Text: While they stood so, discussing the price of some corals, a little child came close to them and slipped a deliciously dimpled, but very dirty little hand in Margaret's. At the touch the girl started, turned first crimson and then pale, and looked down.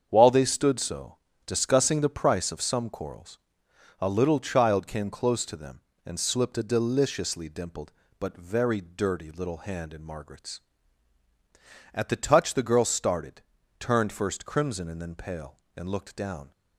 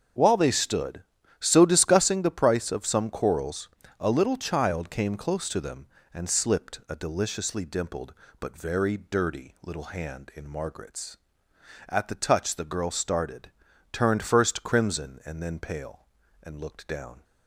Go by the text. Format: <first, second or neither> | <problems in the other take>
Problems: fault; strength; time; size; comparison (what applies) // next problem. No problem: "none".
neither | starts louder than the rest; the same in both